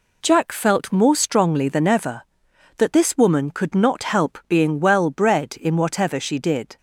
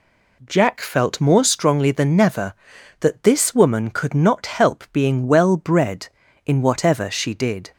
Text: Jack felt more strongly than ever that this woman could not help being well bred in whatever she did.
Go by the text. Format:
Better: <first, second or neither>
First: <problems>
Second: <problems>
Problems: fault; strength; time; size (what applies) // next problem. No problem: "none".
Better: first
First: none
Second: says "never" for "ever"; at 2.1 s